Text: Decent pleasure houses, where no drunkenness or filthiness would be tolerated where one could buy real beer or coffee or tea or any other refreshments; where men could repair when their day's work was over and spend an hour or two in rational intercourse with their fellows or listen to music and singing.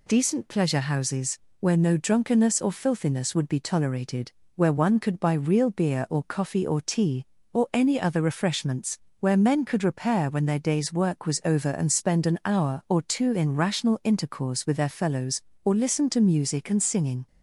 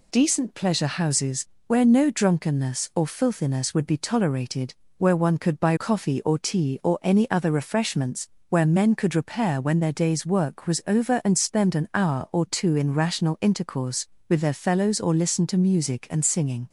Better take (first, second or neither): first